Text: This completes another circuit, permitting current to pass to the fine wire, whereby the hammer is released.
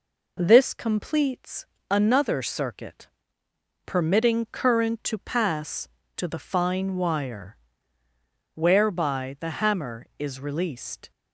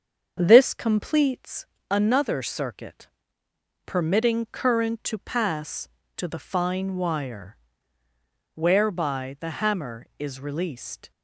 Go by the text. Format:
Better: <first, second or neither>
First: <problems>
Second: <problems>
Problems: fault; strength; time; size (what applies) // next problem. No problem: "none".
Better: first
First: pauses between "completes" and "another"; slight; at 1.6 s; 0.24 s long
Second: starts louder than the rest; until 1.7 s; 7 dB // pauses between "completes" and "another"; slight; at 1.6 s; 0.24 s long